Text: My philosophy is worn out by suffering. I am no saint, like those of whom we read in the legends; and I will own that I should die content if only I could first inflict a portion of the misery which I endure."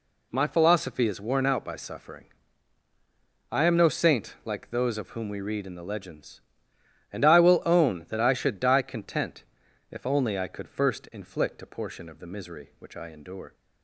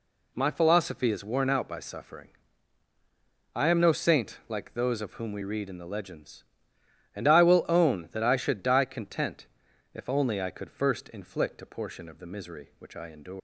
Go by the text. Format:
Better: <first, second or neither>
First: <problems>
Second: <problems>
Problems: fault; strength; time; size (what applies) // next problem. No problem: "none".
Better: first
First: pauses between "content" and "if"; noticeable; at 9.4 s; 0.46 s long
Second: pauses between "content" and "if"; noticeable; at 9.4 s; 0.46 s long // leaves "endure" unfinished; at 13.3 s; 130 ms